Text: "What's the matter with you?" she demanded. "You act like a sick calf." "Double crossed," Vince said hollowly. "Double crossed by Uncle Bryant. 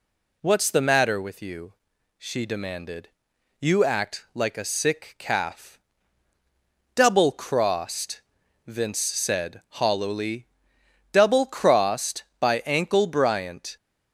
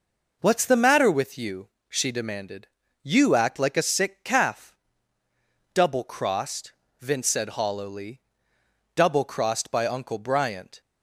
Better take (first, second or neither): second